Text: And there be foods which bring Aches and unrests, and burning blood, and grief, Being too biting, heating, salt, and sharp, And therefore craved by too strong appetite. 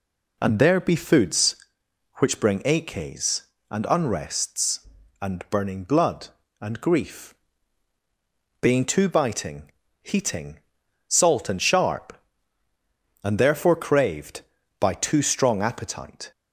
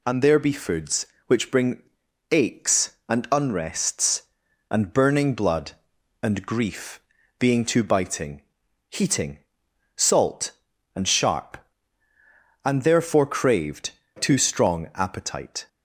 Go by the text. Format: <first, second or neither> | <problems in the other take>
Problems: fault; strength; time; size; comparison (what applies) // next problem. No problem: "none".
first | pauses between "bring" and "Aches"; noticeable; at 1.8 s; 0.48 s long // skips "by"; at 14.0 s